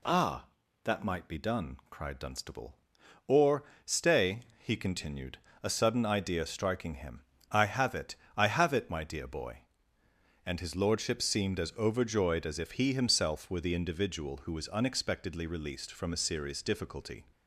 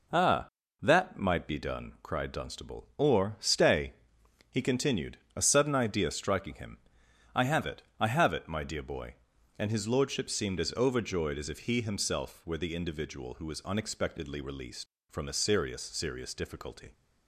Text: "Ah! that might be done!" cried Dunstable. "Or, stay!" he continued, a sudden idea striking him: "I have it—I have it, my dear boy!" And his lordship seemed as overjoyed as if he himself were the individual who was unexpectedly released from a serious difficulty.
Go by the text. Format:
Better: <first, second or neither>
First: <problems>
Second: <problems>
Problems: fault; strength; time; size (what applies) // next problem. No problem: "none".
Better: first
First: none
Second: says "serious" twice; at 15.8 s